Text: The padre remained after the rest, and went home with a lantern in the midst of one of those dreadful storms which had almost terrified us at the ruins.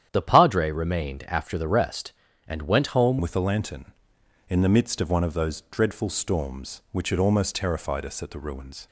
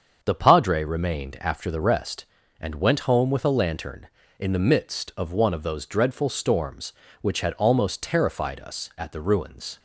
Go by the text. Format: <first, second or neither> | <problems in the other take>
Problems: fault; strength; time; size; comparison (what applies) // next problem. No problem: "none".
second | starts louder than the rest; strong; until 1.1 s; 9.5 dB; also in the second // changes voice at "with"; from 3.1 s on; 5.7 s long